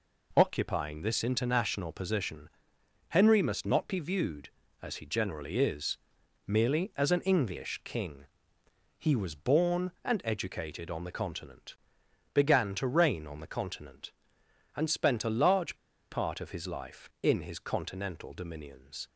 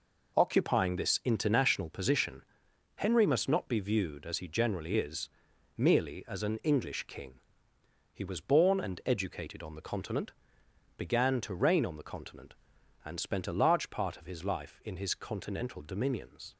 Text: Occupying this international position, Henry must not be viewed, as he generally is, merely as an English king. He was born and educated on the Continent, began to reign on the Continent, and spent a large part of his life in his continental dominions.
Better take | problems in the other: second | pauses between "large" and "part"; slight; at 15.7 s; 0.35 s long

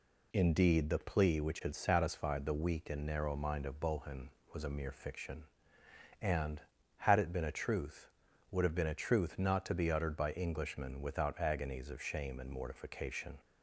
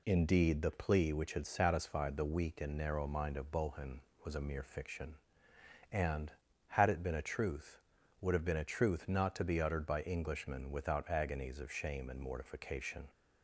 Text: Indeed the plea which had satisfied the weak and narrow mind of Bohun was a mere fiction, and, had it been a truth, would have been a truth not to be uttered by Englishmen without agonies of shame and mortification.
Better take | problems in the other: neither | none

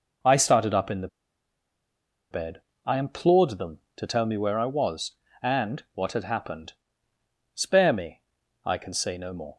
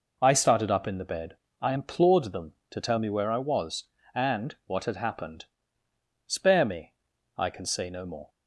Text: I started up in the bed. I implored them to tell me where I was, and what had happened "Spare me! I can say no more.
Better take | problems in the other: second | pauses between "the" and "bed"; at 1.0 s; 1.2 s long // pauses between "happened" and "Spare"; noticeable; at 6.7 s; 0.80 s long; noticeable in the second

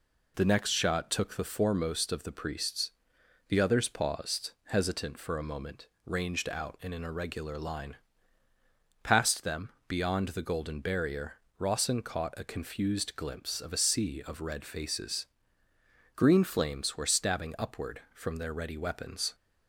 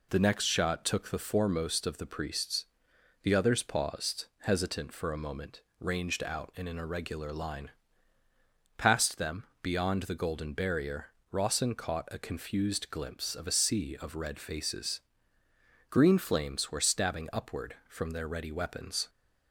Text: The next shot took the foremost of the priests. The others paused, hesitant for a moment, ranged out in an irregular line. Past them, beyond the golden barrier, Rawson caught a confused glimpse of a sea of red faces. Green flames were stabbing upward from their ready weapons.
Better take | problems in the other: neither | none

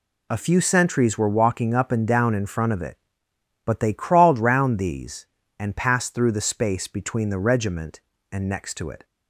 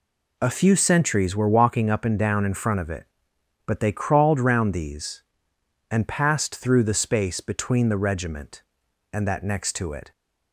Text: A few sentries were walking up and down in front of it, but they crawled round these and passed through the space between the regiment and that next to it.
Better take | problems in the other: second | skips "that"; at 8.4 s

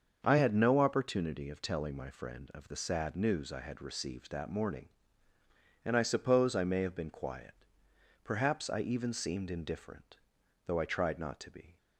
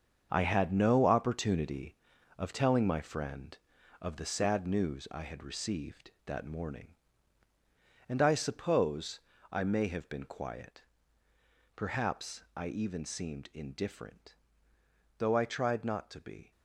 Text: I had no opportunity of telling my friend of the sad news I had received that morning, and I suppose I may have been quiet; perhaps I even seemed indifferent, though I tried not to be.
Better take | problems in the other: first | gets quieter; strong; throughout; 9 dB // starts louder than the rest; until 1.3 s; 7 dB; also in the first // pauses between "suppose" and "I"; slight; at 9.2 s; 0.30 s long

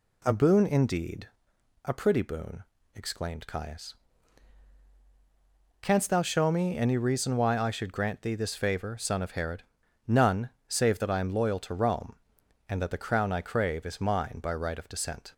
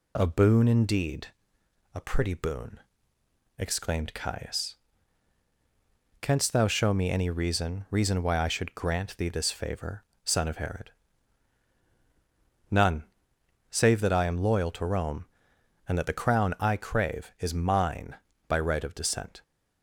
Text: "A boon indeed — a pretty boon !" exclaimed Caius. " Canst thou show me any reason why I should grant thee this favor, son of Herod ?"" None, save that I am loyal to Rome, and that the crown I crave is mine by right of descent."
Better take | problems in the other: first | says "reason" twice; at 7.9 s

